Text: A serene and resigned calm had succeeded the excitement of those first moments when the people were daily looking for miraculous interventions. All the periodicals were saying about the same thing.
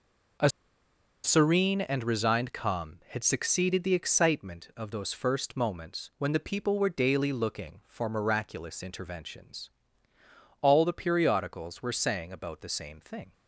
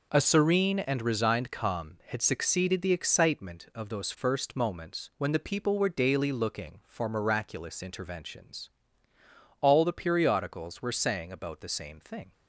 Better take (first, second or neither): second